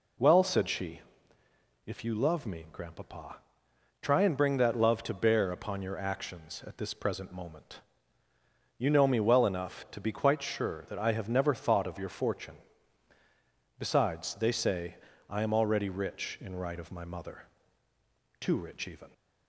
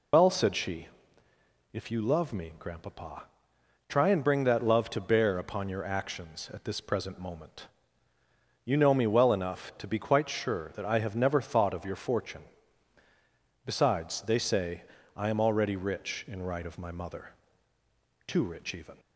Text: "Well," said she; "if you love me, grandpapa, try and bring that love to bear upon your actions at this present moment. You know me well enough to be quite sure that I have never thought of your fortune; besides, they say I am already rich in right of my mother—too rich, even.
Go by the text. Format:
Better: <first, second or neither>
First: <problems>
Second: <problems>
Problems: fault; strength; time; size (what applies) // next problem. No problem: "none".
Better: first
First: pauses between "say" and "I"; slight; at 14.9 s; 0.32 s long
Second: loses the start of "Well"; at 0.1 s; 80 ms // pauses between "say" and "I"; slight; at 14.8 s; 0.32 s long